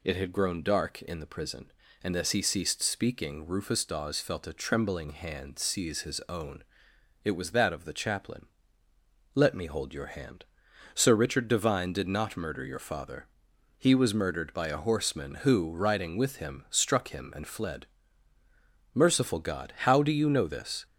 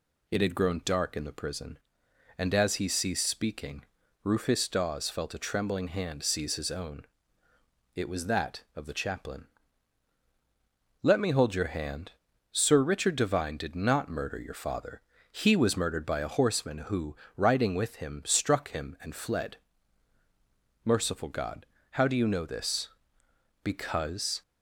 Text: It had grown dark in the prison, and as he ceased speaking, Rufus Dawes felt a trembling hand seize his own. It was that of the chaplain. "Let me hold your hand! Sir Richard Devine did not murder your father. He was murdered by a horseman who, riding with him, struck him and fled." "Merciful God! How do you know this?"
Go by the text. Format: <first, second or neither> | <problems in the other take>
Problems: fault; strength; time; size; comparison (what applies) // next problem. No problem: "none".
first | goes on to say "Because"; noticeable; from 23.6 s on; 0.80 s long